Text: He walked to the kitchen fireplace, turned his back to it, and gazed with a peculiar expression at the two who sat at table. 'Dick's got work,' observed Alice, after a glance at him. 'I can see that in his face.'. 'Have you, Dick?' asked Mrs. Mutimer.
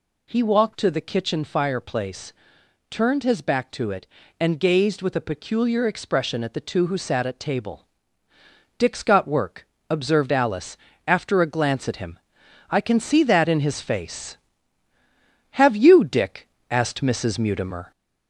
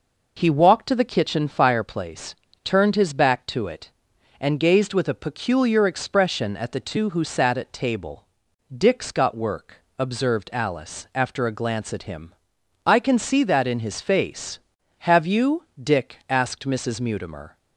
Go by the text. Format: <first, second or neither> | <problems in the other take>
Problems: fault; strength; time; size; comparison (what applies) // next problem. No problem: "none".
second | gets louder; slight; throughout; 3 dB